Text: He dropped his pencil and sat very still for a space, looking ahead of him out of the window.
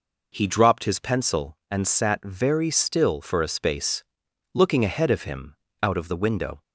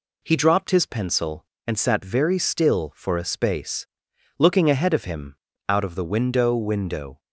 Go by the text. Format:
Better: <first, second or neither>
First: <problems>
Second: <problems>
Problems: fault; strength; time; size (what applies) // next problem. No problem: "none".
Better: first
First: pauses between "him" and "out"; slight; at 5.5 s; 0.30 s long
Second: pauses between "him" and "out"; slight; at 5.3 s; 0.32 s long // says "window" twice; at 6.5 s